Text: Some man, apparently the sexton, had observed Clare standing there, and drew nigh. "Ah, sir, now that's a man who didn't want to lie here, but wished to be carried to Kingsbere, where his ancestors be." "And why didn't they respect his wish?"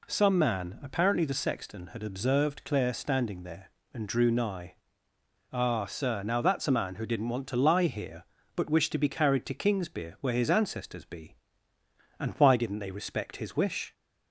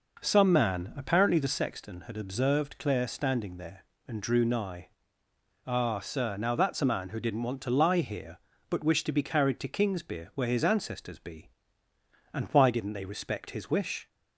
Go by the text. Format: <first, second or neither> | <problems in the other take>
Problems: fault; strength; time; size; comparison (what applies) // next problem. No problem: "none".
first | starts louder than the rest; noticeable; until 1.6 s; 5 dB